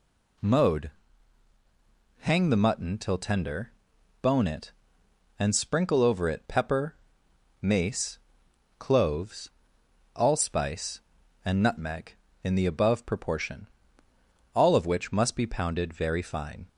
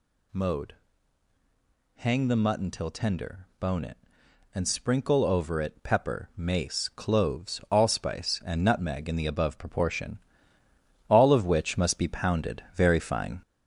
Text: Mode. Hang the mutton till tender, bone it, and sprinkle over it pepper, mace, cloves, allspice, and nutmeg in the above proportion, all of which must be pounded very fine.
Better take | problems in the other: first | gets louder; noticeable; throughout; 5.5 dB

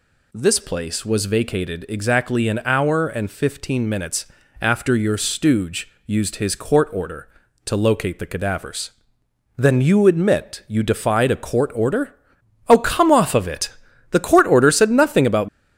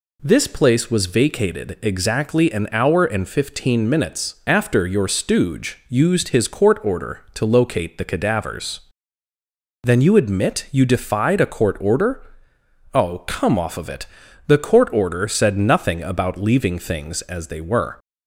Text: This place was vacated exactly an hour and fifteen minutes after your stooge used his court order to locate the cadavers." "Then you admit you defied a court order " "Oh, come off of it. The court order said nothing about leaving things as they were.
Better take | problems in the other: second | pauses between "minutes" and "after"; slight; at 4.2 s; 0.36 s long // pauses between "stooge" and "used"; slight; at 5.8 s; 0.16 s long // stops before "leaving things as they were"; at 15.4 s

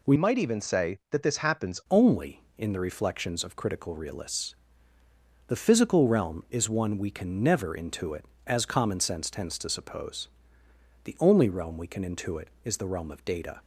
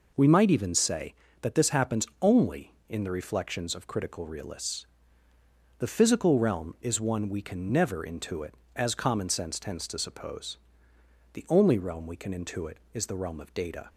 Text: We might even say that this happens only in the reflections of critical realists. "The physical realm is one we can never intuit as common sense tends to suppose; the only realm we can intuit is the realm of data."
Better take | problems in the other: second | changes voice from "might" to "happens"; from 0.1 to 1.7 s; 1.6 s long

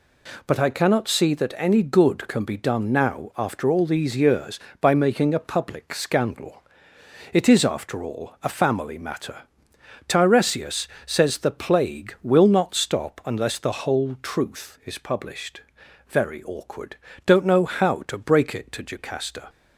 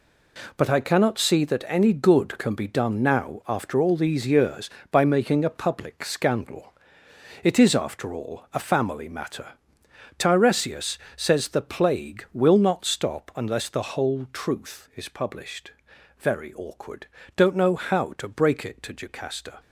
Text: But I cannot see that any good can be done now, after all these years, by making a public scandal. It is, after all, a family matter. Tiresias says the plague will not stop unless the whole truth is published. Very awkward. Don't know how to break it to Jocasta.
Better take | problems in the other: first | gets quieter; strong; throughout; 8.5 dB // pauses between "Tiresias" and "says"; slight; at 10.9 s; 0.18 s long; slight in the first

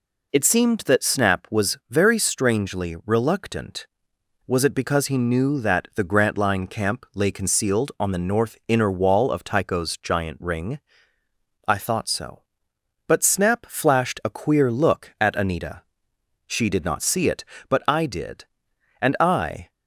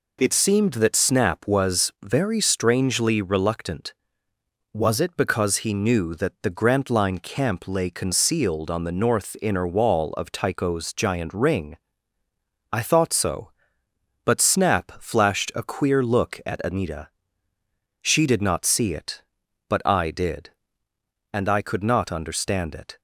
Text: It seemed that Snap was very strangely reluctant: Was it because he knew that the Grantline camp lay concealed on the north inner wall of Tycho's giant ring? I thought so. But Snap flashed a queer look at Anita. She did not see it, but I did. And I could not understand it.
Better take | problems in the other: second | stops before "could not understand it"; at 19.7 s

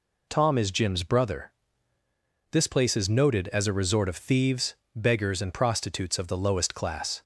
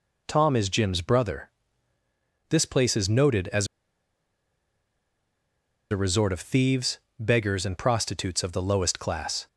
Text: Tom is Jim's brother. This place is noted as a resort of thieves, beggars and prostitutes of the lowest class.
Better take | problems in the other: first | pauses between "as" and "a"; strong; at 3.6 s; 2.2 s long

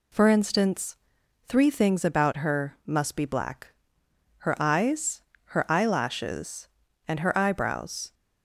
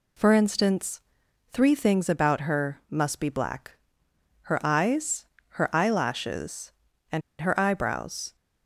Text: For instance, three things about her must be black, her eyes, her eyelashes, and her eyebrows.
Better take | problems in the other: first | pauses between "and" and "her"; slight; at 7.2 s; 0.19 s long

